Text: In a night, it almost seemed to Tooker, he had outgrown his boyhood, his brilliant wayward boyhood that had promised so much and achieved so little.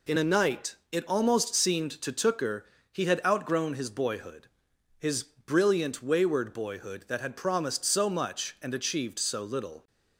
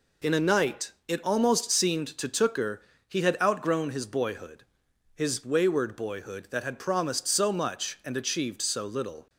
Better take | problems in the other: first | skips "brilliant"; at 5.4 s

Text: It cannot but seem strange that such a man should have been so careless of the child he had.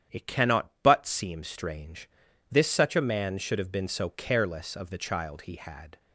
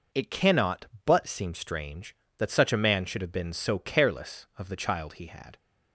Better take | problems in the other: second | starts louder than the rest; strong; until 1.2 s; 9.5 dB // says "this" for "that"; at 2.5 s

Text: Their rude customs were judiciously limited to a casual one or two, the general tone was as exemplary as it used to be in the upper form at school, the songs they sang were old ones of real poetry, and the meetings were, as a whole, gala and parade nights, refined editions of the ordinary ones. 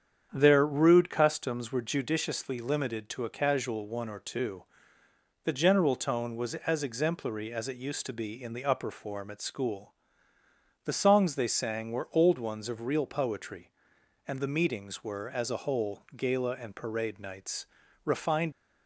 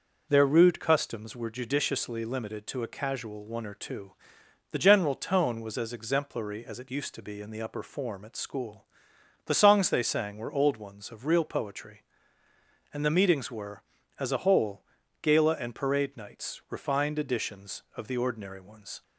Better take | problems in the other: second | starts louder than the rest; strong; until 1.3 s; 8 dB // stops before "editions of the ordinary ones"; at 18.5 s

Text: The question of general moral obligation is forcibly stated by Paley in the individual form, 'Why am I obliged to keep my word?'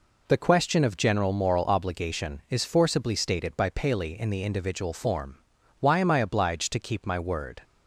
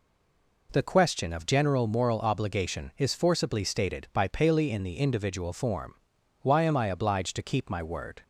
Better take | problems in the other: first | stays silent before the first word; slight; until 0.6 s; 0.6 s long

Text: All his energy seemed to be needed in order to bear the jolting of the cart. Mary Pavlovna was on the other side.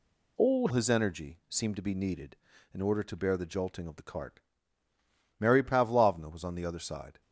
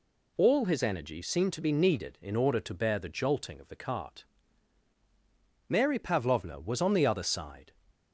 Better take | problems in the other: second | changes voice at "his"; from 0.7 s on; 6.5 s long

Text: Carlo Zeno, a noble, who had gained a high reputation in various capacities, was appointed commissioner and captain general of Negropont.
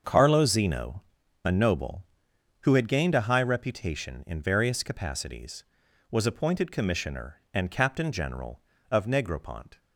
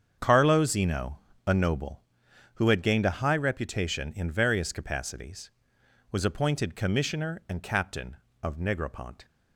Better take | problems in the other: first | starts louder than the rest; strong; until 1.1 s; 7.5 dB; also in the first // skips "general"; at 8.2 s

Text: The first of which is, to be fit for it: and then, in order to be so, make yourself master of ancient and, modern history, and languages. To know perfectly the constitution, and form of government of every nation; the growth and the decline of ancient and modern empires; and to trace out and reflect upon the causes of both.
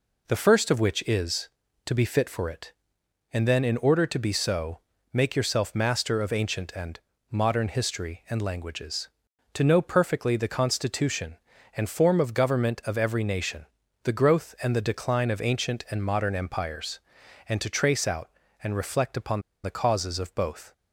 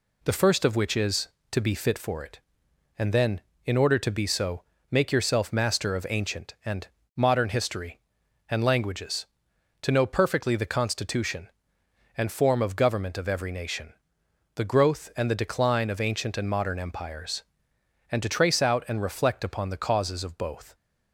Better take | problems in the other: second | pauses between "upon" and "the"; slight; at 19.4 s; 0.22 s long

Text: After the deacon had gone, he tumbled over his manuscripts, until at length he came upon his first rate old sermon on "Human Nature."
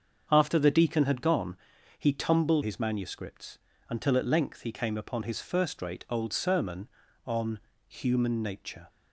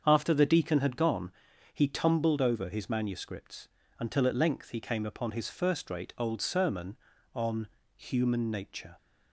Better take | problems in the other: second | starts louder than the rest; until 1.3 s; 7 dB; also in the second // skips "over"; at 2.6 s // pauses between "on" and "Human"; slight; at 7.5 s; 0.28 s long; slight in the second

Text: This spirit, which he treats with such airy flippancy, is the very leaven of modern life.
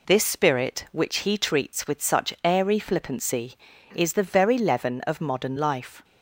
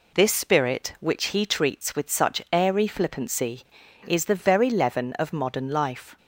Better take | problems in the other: neither | none

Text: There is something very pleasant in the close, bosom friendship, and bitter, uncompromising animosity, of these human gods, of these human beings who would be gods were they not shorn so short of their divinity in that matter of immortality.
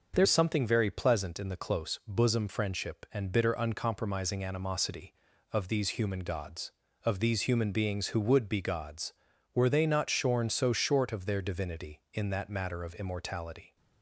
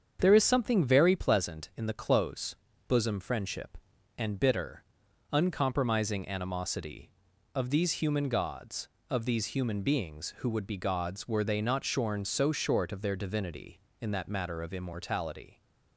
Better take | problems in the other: second | starts louder than the rest; noticeable; until 1.1 s; 6 dB; strong in the second // changes voice at "is"; from 0.2 s on; 13.5 s long

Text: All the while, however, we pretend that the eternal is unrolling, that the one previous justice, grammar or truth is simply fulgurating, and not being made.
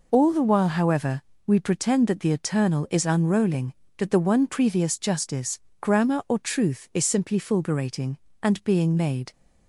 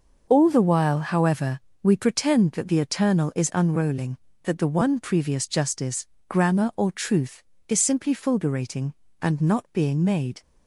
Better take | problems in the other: second | skips "not"; at 8.6 s

